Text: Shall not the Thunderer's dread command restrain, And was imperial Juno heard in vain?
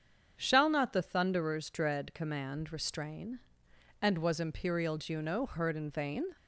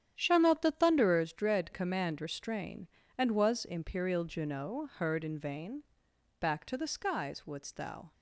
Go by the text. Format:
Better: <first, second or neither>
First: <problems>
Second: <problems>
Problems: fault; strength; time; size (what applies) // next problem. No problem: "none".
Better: first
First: starts louder than the rest; strong; until 1.4 s; 7.5 dB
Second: starts louder than the rest; strong; until 1.1 s; 9.5 dB // goes on to say "Back to the skies wouldst thou"; strong; from 6.3 s on; 1.7 s long